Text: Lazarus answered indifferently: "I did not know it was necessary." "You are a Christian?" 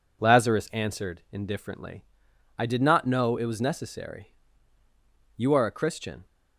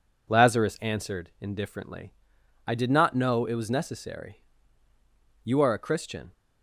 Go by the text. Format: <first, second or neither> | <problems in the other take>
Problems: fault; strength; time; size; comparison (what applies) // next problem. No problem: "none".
neither | none